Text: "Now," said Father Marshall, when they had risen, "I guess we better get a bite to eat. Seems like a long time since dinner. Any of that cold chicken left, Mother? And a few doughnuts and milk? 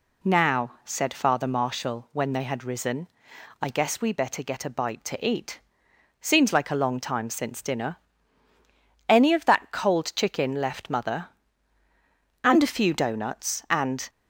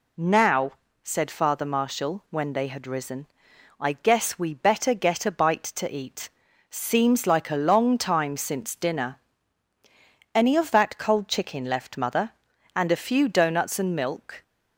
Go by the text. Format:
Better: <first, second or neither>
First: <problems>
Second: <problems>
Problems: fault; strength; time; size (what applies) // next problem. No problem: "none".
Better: second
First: stops before "milk"; at 14.0 s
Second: none